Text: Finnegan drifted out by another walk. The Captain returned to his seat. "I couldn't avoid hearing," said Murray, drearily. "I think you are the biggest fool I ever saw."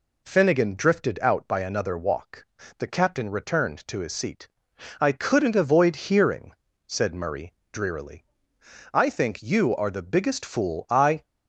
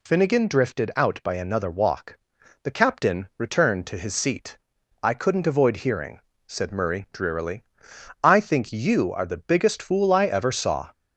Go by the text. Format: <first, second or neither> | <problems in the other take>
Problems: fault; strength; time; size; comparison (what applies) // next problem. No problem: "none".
second | stops before "ever saw"; at 11.2 s